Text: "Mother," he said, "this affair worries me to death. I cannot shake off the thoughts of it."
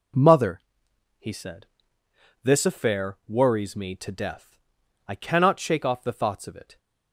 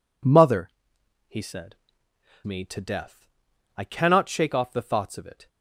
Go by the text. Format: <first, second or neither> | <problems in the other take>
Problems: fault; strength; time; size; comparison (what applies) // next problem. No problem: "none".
first | skips "this affair worries"; at 2.0 s